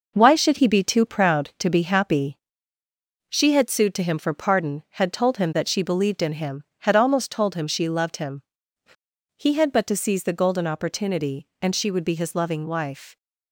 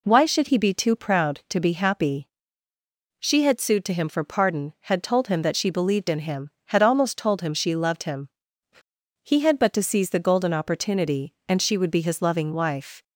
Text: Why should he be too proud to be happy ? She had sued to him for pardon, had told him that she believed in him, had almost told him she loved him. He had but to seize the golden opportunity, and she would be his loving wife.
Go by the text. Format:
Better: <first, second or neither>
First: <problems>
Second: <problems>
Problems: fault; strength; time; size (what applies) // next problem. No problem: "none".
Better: second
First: gets quieter; throughout; 6.5 dB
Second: none